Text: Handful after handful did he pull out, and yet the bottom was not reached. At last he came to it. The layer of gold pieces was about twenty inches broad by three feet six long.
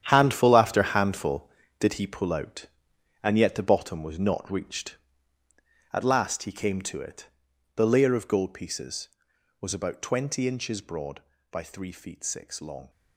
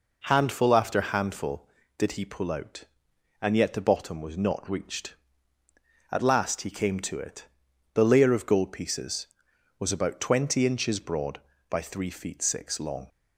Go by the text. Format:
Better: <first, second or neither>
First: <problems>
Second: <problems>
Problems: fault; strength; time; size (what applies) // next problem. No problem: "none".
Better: second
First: gets quieter; strong; throughout; 12 dB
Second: none